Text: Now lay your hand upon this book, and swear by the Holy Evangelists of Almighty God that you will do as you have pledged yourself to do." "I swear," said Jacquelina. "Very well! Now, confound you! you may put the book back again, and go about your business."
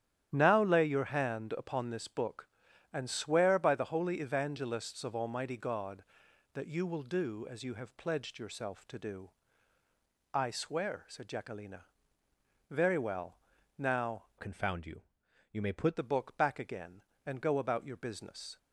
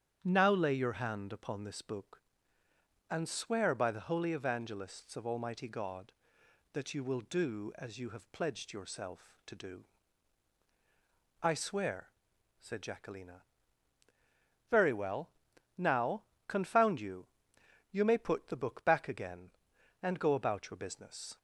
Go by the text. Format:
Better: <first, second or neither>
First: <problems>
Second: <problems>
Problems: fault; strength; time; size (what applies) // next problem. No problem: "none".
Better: second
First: starts louder than the rest; strong; until 1.3 s; 11 dB // changes voice from "confound" to "put"; from 14.3 to 15.9 s; 1.6 s long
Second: starts louder than the rest; strong; until 1.2 s; 8.5 dB